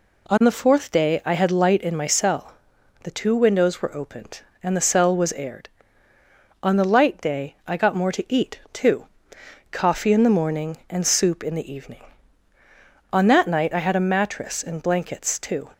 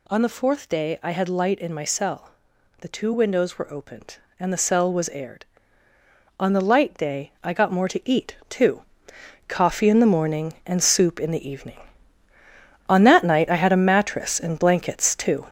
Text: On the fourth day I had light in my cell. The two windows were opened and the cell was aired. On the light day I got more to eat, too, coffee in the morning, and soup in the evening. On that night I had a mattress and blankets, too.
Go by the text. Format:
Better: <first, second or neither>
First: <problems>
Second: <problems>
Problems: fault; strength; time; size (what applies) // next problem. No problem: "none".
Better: first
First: none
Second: gets louder; throughout; 6.5 dB